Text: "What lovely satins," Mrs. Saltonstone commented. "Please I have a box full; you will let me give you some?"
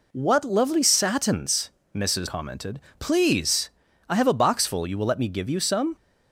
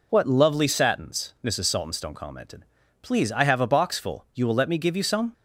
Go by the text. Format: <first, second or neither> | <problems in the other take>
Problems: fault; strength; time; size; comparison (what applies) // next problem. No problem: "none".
second | skips "Saltonstone"; at 2.2 s // pauses between "Please" and "I"; slight; at 3.7 s; 0.36 s long